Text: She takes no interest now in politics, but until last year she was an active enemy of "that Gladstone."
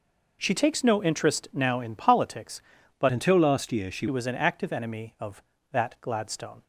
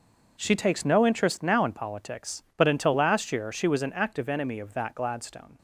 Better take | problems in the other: second | changes voice from "until" to "she"; from 3.1 to 4.0 s; 0.9 s long

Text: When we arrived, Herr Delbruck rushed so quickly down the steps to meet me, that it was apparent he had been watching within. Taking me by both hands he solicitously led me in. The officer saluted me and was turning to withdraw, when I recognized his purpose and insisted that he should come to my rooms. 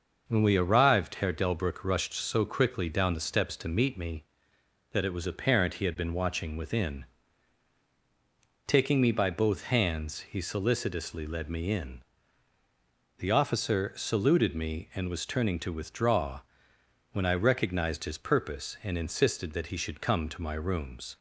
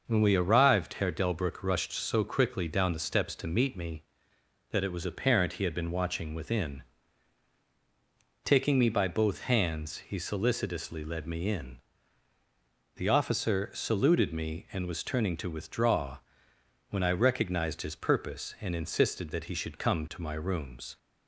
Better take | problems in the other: neither | starts louder than the rest; noticeable; the same in both

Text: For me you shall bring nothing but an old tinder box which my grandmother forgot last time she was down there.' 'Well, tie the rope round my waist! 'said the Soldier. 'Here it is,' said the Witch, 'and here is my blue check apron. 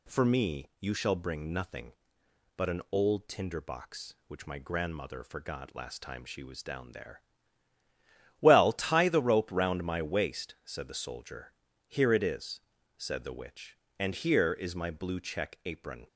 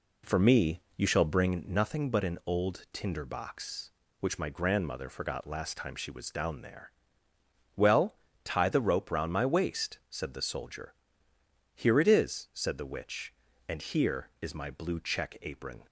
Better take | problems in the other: first | starts louder than the rest; slight; until 1.7 s; 3 dB // pauses between "me" and "you"; slight; at 0.8 s; 0.16 s long

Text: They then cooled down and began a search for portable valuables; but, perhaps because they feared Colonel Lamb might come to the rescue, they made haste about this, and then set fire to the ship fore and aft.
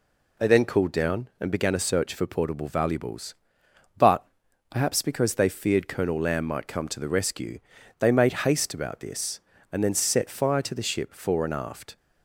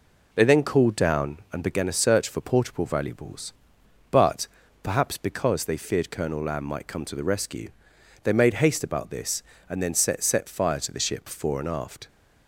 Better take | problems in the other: first | says "set" twice; at 10.2 s

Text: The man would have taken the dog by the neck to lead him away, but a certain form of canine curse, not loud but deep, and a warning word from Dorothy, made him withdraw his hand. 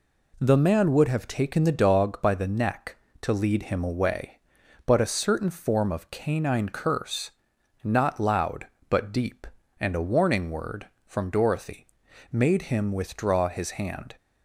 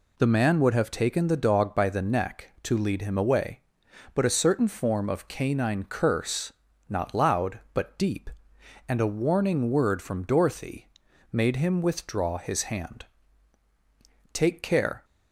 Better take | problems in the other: first | goes on to say "Take care"; noticeable; from 14.3 s on; 0.72 s long

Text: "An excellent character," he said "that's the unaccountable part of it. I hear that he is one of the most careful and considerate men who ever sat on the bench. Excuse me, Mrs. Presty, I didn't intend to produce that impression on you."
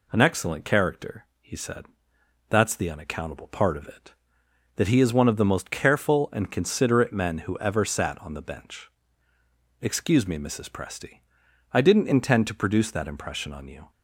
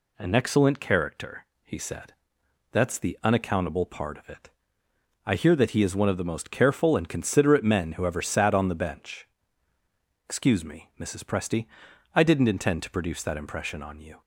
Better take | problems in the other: second | pauses between "said" and "that's"; noticeable; at 1.8 s; 0.62 s long; noticeable in the second // skips "I hear"; at 4.4 s

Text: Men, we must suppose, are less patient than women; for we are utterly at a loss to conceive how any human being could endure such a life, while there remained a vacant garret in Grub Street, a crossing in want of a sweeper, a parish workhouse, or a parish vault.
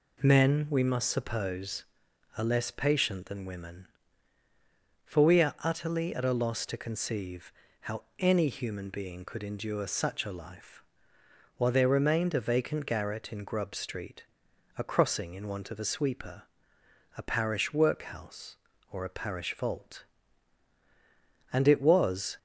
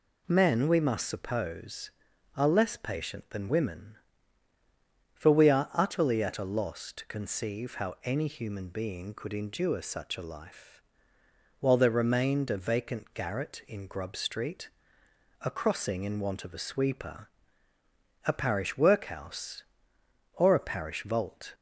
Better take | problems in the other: second | pauses between "conceive" and "how"; slight; at 7.5 s; 0.28 s long // goes on to say "And it was"; noticeable; from 21.5 s on; 0.86 s long

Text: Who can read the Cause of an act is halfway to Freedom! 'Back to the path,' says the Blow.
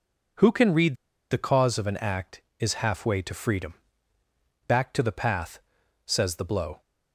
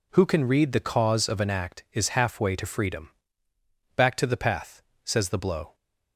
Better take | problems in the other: second | pauses between "read" and "the"; slight; at 0.9 s; 0.34 s long

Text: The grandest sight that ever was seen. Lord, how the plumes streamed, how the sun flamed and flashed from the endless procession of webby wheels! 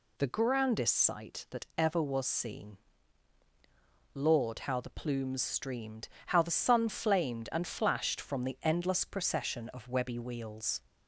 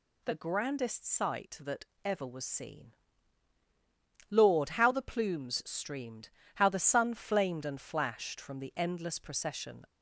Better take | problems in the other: first | pauses between "that" and "ever"; slight; at 1.8 s; 0.20 s long // stops before "of webby wheels"; at 9.8 s

